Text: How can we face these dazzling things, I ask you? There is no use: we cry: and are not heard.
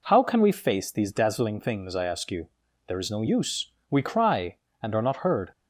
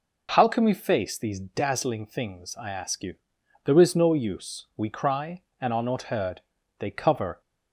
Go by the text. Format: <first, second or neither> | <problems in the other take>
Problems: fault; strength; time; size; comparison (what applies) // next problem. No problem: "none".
first | goes on to say "They cover"; from 6.8 s on; 0.60 s long